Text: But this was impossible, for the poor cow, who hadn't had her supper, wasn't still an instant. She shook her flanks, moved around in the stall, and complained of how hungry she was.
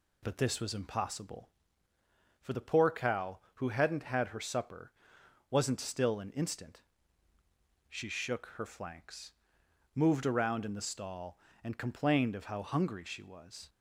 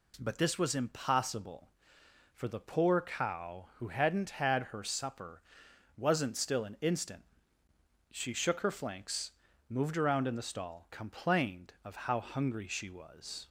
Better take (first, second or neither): first